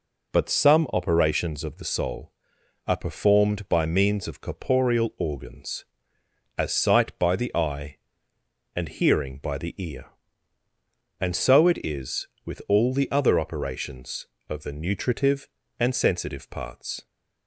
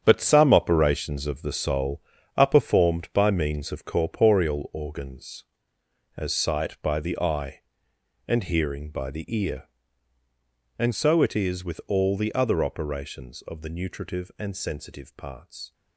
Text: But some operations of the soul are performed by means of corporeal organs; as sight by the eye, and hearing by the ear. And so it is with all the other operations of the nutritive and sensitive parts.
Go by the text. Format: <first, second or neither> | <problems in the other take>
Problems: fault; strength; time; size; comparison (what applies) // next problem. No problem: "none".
first | gets quieter; strong; throughout; 10 dB